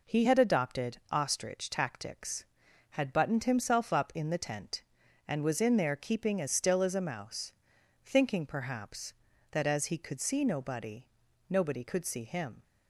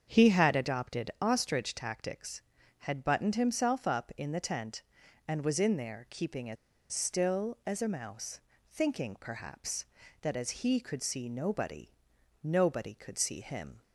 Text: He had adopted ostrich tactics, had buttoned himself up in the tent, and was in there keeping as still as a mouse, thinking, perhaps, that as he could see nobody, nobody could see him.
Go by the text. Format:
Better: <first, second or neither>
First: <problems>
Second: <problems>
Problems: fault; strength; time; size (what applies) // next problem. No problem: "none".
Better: first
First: none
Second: starts louder than the rest; until 1.1 s; 7 dB // pauses between "as" and "still"; at 6.5 s; 0.36 s long